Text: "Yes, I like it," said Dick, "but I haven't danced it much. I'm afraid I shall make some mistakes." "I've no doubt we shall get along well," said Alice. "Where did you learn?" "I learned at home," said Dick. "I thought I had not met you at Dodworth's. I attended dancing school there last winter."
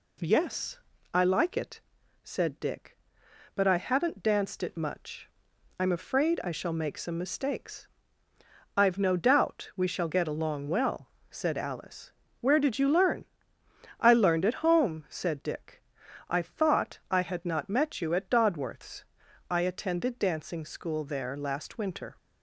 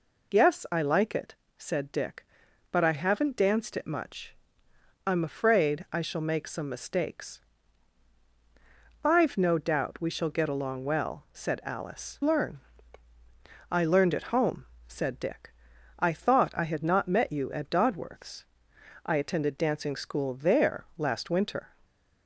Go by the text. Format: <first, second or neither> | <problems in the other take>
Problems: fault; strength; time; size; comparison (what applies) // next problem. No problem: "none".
first | skips "Where did you"; at 12.2 s